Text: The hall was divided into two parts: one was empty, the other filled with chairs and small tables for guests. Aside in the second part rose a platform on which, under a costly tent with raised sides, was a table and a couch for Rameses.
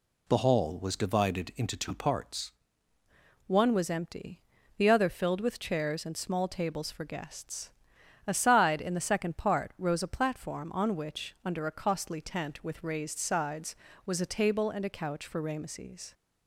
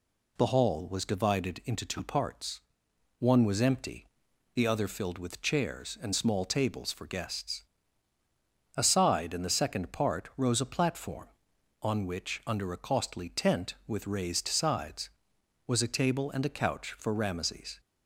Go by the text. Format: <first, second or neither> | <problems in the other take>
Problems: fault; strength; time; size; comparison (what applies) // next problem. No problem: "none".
second | changes voice at "one"; from 3.4 s on; 12.7 s long